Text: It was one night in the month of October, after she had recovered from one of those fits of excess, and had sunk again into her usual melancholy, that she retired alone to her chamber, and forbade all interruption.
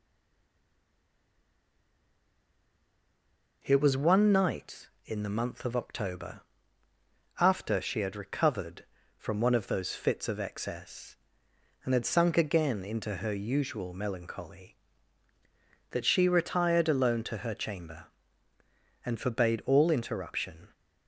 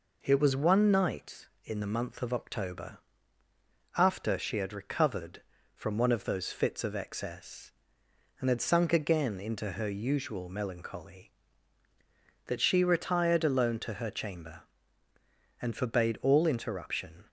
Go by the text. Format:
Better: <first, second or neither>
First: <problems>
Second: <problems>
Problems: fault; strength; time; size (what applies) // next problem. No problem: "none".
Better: second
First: stays silent before the first word; strong; until 3.6 s; 3.6 s long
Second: none